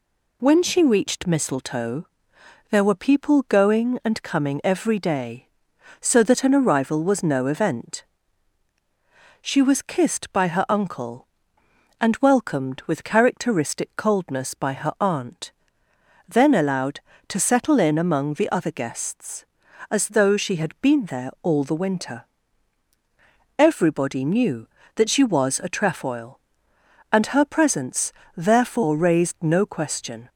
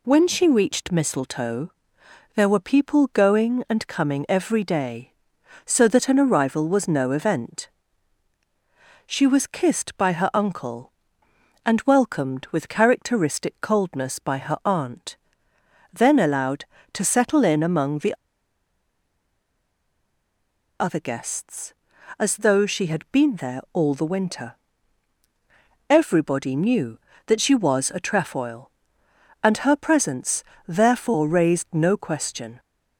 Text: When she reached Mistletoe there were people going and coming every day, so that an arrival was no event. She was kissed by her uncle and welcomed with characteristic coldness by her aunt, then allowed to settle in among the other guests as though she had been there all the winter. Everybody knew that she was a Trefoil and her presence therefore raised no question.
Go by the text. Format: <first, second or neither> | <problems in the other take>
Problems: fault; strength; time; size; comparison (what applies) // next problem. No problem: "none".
first | pauses between "Mistletoe" and "there"; noticeable; at 1.7 s; 0.64 s long; noticeable in the first // pauses between "the" and "other"; strong; at 18.1 s; 2.6 s long // pauses between "presence" and "therefore"; slight; at 30.4 s; 0.24 s long; slight in the first